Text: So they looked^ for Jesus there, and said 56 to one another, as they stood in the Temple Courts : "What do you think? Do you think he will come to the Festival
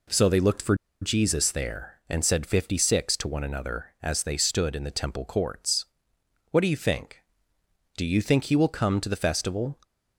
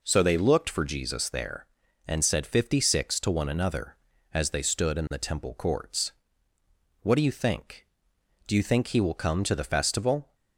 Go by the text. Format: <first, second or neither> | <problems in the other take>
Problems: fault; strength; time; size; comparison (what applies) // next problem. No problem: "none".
second | pauses between "for" and "Jesus"; slight; at 0.7 s; 0.27 s long